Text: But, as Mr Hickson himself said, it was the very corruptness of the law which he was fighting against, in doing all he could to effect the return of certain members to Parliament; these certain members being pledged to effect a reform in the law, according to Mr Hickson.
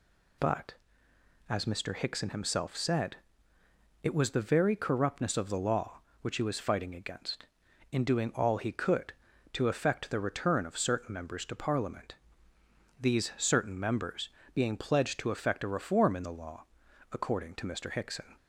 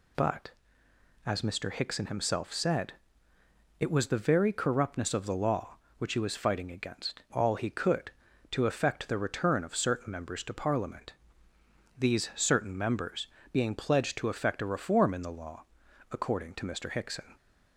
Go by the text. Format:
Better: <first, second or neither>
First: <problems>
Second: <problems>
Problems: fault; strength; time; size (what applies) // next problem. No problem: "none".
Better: first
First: pauses between "members" and "being"; slight; at 14.2 s; 0.24 s long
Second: skips "in doing"; at 7.2 s // pauses between "members" and "being"; slight; at 13.2 s; 0.24 s long